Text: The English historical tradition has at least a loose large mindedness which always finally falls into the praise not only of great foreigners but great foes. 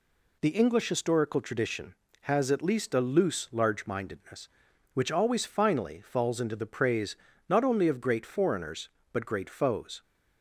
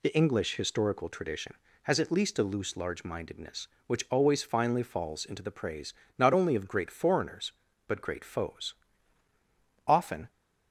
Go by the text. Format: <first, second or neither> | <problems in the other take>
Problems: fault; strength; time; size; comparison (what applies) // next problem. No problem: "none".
first | pauses between "praise" and "not"; slight; at 5.9 s; 0.26 s long; slight in the first // goes on to say "Often"; slight; from 9.8 s on; 0.44 s long